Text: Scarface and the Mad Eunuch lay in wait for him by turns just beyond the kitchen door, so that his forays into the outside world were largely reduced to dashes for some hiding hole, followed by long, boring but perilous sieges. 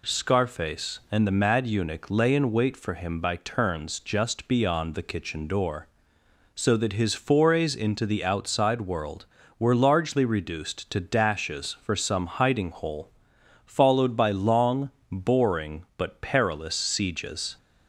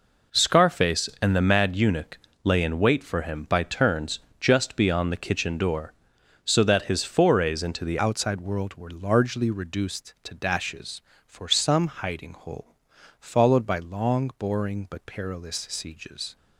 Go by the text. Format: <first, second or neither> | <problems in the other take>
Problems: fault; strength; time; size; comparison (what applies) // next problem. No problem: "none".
first | pauses between "Eunuch" and "lay"; slight; at 2.1 s; 0.24 s long // pauses between "turns" and "just"; slight; at 4.1 s; 0.20 s long // changes voice at "outside"; from 7.9 s on; 8.4 s long